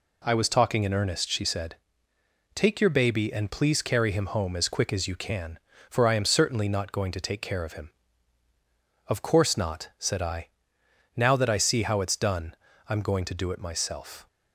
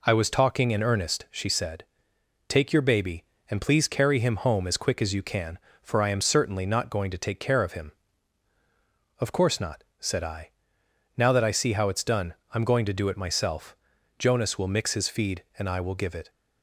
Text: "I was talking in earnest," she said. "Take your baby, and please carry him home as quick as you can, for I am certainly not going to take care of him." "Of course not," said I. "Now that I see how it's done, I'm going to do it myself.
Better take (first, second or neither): first